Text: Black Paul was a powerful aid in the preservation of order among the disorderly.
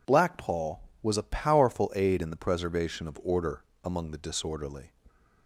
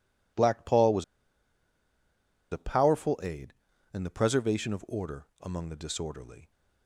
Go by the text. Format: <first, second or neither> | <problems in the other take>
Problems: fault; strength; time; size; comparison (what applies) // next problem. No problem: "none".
first | pauses between "was" and "a"; strong; at 1.0 s; 1.4 s long // pauses between "order" and "among"; slight; at 5.2 s; 0.16 s long; slight in the first